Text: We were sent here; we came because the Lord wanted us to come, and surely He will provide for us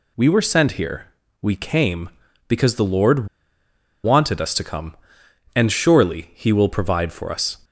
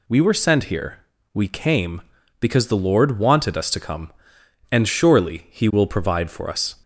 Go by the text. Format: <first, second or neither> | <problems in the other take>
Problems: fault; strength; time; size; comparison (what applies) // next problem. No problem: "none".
second | pauses between "Lord" and "wanted"; noticeable; at 3.2 s; 0.78 s long